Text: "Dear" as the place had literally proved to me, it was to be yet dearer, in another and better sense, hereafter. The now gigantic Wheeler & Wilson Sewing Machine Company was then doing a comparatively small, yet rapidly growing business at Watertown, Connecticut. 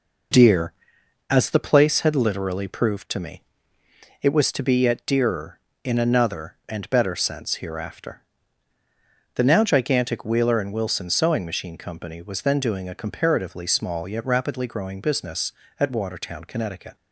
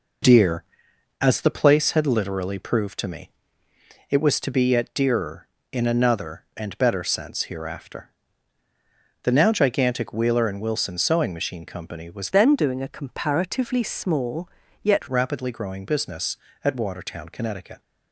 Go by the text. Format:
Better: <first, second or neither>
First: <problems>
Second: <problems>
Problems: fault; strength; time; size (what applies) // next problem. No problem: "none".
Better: first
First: none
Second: changes voice from "then" to "yet"; from 12.3 to 15.0 s; 2.7 s long